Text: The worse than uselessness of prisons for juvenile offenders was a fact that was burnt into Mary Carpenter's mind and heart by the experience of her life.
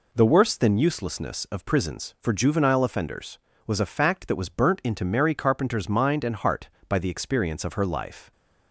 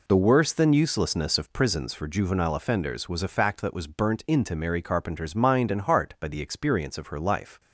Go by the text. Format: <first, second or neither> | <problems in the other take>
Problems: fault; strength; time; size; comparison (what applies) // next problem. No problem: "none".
neither | none